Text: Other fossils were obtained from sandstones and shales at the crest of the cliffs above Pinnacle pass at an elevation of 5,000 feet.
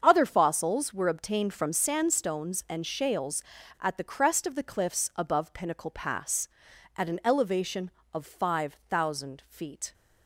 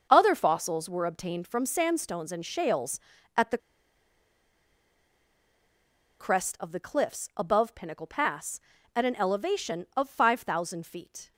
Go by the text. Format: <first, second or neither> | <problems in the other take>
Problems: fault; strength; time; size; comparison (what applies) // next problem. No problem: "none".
first | starts louder than the rest; until 1.1 s; 6.5 dB; also in the first // pauses between "the" and "crest"; strong; at 3.5 s; 2.6 s long